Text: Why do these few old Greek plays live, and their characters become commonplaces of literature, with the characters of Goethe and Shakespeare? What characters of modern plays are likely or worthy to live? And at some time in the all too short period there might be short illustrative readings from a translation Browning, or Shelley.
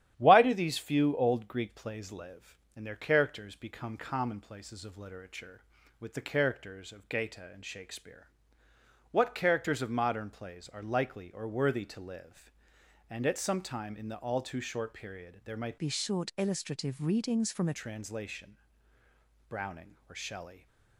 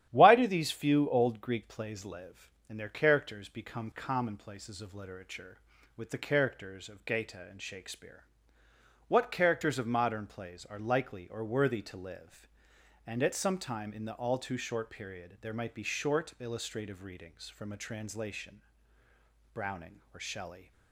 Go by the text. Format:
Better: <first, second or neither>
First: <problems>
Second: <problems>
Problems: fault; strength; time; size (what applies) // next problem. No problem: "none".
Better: second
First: starts louder than the rest; strong; until 1.1 s; 11 dB // changes voice from "be" to "a"; from 15.7 to 17.7 s; 2.0 s long // pauses between "translation" and "Browning"; noticeable; at 18.5 s; 0.90 s long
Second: starts louder than the rest; strong; until 1.1 s; 11 dB // pauses between "translation" and "Browning"; noticeable; at 18.6 s; 0.90 s long